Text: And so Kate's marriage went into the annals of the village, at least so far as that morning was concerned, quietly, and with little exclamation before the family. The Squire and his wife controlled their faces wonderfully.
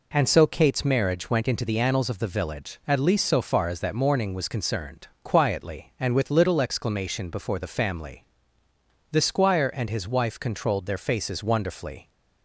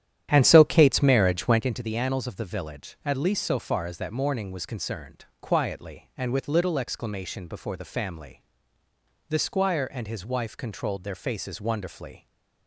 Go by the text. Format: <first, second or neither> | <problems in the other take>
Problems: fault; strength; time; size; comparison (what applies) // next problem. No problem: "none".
first | starts louder than the rest; strong; until 1.7 s; 11 dB